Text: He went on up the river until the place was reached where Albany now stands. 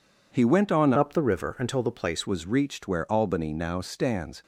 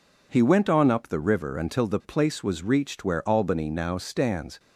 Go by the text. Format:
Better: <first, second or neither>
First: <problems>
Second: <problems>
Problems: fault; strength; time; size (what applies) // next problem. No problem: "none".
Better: second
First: changes voice from "up" to "place"; from 0.9 to 2.2 s; 1.3 s long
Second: none